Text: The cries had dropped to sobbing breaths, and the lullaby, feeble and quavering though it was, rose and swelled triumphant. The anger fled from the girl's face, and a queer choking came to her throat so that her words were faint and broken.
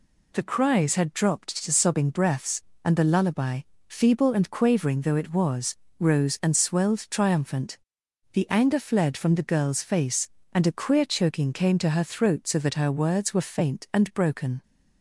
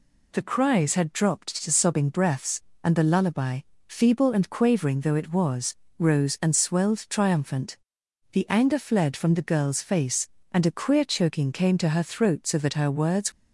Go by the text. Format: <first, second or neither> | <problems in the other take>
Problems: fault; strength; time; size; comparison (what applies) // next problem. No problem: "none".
first | stops before "were faint and broken"; at 13.3 s